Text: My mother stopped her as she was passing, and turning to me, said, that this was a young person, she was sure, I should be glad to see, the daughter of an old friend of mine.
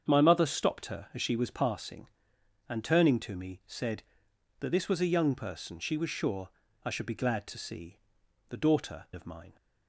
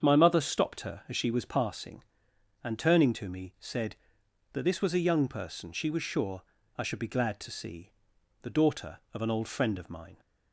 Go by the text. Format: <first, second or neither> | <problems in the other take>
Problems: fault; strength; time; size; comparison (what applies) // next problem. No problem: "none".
second | starts louder than the rest; strong; until 1.0 s; 7.5 dB; strong in the second // skips "of an old friend"; at 9.1 s